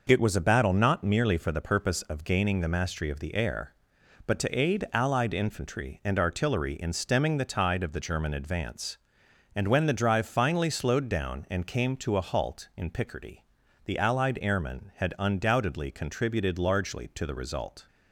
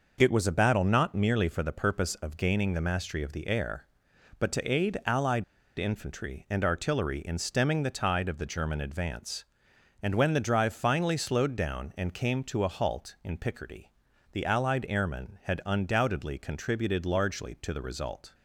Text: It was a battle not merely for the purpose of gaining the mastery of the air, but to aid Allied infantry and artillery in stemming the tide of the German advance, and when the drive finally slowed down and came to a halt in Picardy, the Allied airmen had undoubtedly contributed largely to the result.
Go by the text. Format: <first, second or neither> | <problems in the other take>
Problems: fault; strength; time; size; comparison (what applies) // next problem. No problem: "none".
first | pauses between "Allied" and "infantry"; slight; at 5.4 s; 0.35 s long